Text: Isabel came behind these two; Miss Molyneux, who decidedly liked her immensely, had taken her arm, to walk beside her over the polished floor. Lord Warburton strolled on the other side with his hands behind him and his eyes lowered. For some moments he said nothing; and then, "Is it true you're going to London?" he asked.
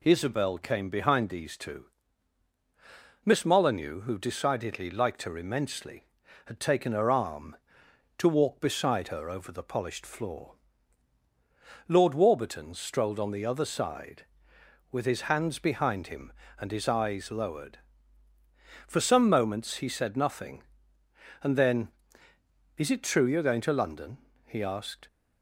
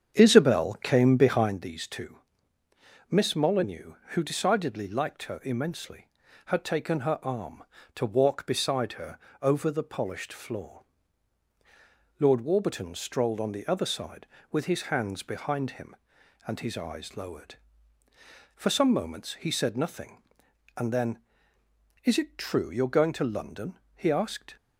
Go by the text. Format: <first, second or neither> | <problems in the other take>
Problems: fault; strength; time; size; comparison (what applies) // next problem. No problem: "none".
first | starts louder than the rest; strong; until 1.6 s; 8 dB // pauses between "her" and "over"; slight; at 9.1 s; 0.20 s long